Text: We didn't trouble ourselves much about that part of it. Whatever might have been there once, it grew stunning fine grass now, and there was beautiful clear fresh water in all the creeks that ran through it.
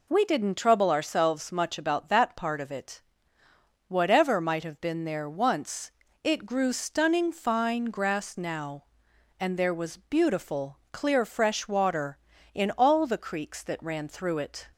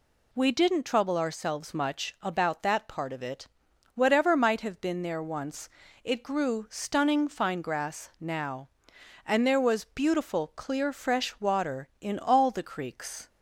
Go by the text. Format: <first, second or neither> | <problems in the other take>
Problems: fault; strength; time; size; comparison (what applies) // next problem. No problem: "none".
first | stops before "that ran through it"; at 13.2 s